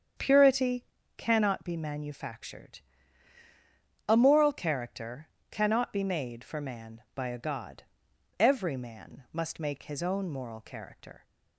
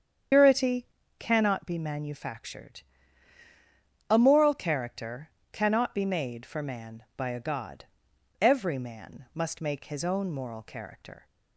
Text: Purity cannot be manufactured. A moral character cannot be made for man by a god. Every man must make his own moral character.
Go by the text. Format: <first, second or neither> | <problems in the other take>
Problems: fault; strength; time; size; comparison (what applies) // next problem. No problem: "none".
first | loses the start of "Purity"; at 0.3 s; 125 ms // starts louder than the rest; strong; until 1.6 s; 8 dB; strong in the first // pauses between "Purity" and "cannot"; slight; at 0.8 s; 0.32 s long; slight in the first // pauses between "character" and "cannot"; slight; at 5.2 s; 0.24 s long; slight in the first